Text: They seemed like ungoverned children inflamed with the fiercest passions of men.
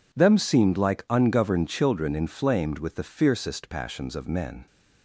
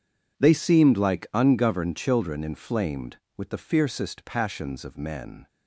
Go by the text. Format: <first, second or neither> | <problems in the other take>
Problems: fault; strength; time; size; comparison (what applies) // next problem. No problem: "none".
second | says "Them" for "They"; at 0.1 s